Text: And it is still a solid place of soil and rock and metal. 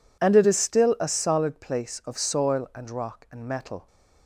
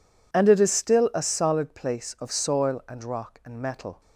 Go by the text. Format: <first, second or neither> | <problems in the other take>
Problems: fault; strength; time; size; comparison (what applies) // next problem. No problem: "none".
neither | none